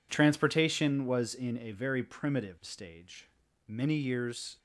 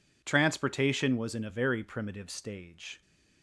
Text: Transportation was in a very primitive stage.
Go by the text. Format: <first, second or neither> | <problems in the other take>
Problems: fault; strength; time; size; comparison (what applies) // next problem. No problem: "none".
second | goes on to say "Many years"; noticeable; from 3.6 s on; 0.92 s long